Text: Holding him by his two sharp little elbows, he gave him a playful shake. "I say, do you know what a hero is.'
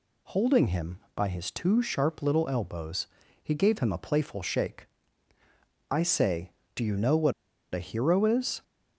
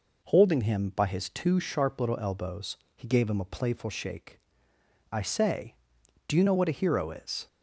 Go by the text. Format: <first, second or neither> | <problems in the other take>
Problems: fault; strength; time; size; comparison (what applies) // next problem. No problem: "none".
second | pauses between "what" and "a"; at 7.3 s; 0.41 s long